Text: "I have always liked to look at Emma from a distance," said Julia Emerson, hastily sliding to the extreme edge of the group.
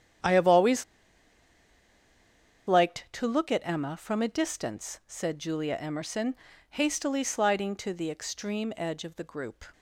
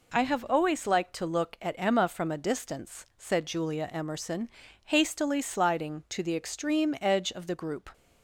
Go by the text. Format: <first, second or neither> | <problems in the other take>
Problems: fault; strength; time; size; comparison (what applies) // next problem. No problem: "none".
second | starts louder than the rest; strong; until 3.1 s; 9.5 dB // pauses between "always" and "liked"; strong; at 0.8 s; 1.8 s long